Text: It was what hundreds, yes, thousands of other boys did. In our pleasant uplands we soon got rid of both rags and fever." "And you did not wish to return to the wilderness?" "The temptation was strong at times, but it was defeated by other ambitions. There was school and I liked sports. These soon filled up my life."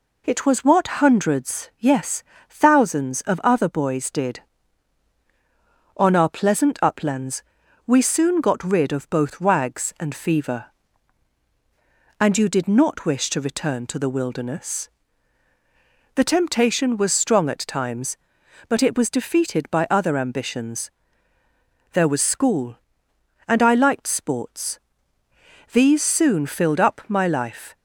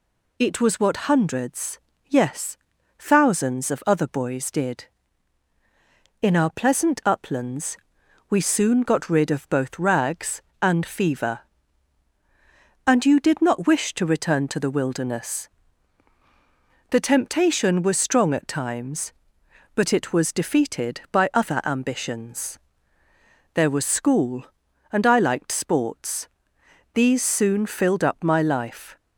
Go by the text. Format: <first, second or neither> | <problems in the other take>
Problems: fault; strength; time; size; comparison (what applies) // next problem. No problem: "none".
second | says "On" for "In"; at 5.9 s // pauses between "uplands" and "we"; at 7.4 s; 0.44 s long; noticeable in the second